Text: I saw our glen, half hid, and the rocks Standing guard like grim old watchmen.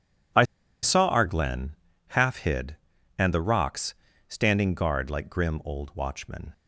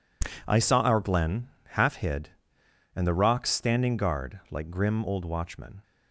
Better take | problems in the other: second | pauses between "I" and "saw"; at 0.4 s; 0.39 s long // pauses between "rocks" and "Standing"; slight; at 3.9 s; 0.34 s long

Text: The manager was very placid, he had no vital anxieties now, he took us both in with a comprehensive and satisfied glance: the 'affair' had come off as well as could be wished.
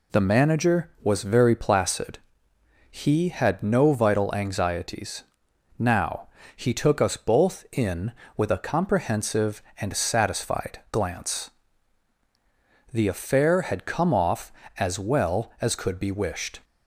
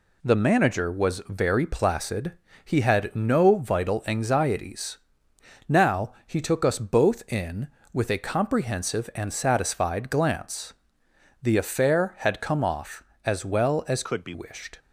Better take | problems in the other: first | pauses between "anxieties" and "now"; noticeable; at 4.9 s; 0.68 s long; noticeable in the first // changes voice from "could" to "be"; from 14.0 to 14.3 s; 0.3 s long

